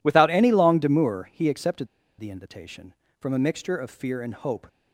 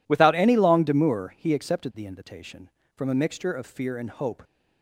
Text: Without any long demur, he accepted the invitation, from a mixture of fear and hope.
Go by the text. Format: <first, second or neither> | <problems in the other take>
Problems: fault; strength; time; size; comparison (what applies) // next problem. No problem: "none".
second | pauses between "accepted" and "the"; slight; at 1.8 s; 0.32 s long